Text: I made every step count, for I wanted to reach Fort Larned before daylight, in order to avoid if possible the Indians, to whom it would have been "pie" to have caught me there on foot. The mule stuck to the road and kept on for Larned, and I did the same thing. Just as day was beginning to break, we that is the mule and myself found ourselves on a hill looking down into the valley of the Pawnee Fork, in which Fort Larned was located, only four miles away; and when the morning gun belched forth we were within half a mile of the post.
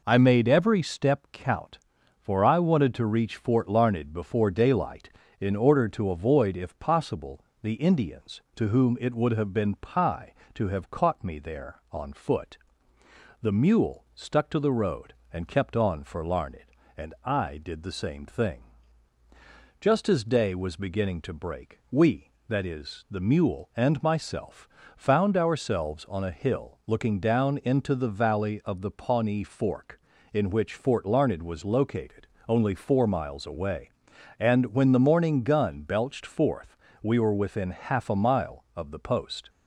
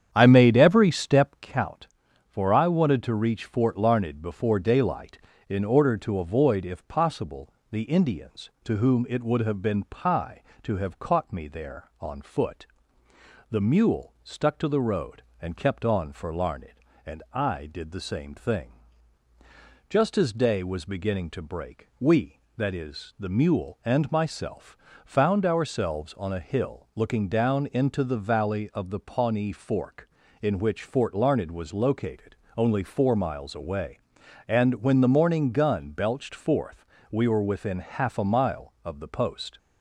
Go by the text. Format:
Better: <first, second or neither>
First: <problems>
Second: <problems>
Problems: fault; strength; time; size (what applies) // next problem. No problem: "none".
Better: first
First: pauses between "possible" and "the"; slight; at 7.4 s; 0.18 s long // pauses between "myself" and "found"; slight; at 24.6 s; 0.30 s long // pauses between "forth" and "we"; slight; at 36.7 s; 0.24 s long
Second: starts louder than the rest; strong; until 1.5 s; 8.5 dB // pauses between "possible" and "the"; slight; at 7.5 s; 0.18 s long // pauses between "myself" and "found"; slight; at 24.7 s; 0.30 s long // pauses between "forth" and "we"; slight; at 36.8 s; 0.24 s long